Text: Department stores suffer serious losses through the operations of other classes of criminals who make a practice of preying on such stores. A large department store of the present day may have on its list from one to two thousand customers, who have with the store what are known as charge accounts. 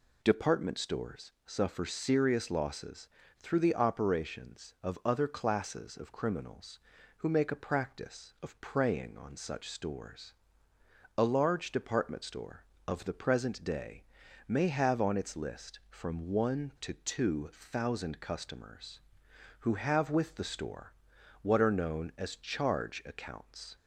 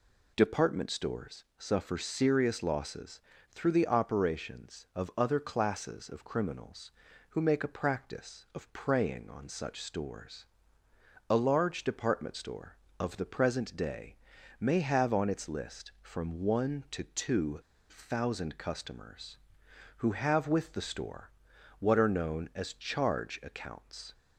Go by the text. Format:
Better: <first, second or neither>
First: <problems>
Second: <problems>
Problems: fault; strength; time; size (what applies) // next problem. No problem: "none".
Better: first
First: pauses between "losses" and "through"; slight; at 3.0 s; 0.30 s long // pauses between "day" and "may"; at 14.0 s; 0.42 s long // pauses between "store" and "what"; noticeable; at 20.9 s; 0.48 s long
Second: pauses between "losses" and "through"; slight; at 3.1 s; 0.30 s long // pauses between "day" and "may"; at 14.1 s; 0.42 s long // pauses between "two" and "thousand"; slight; at 17.5 s; 0.29 s long // pauses between "store" and "what"; noticeable; at 21.3 s; 0.48 s long